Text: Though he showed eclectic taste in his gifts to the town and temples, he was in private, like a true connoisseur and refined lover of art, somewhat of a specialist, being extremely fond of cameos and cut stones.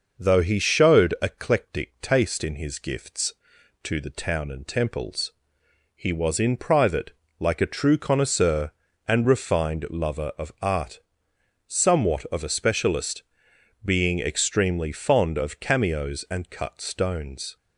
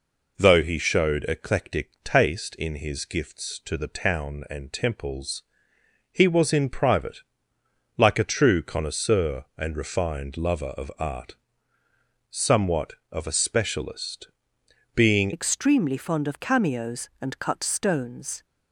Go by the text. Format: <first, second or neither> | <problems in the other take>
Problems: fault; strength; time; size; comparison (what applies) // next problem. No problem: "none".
first | changes voice at "extremely"; from 15.3 s on; 3.1 s long